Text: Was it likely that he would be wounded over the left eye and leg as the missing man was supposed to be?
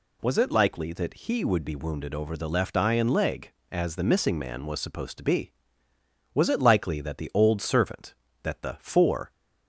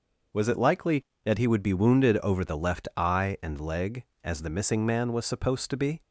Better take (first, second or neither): second